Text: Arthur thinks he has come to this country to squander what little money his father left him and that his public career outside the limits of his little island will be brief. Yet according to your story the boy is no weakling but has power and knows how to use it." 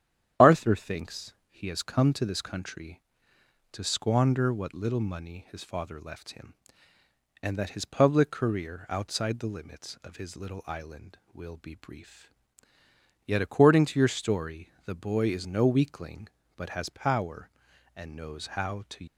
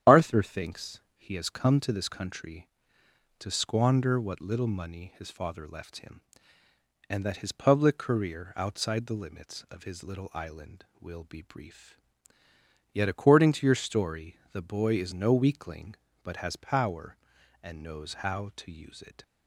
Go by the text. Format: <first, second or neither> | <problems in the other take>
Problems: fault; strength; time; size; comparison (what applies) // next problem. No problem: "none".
second | starts louder than the rest; strong; until 1.5 s; 10 dB; strong in the second // pauses between "thinks" and "he"; slight; at 1.3 s; 0.16 s long; slight in the second // pauses between "story" and "the"; slight; at 14.6 s; 0.16 s long; slight in the second // stops before "use it"; at 19.0 s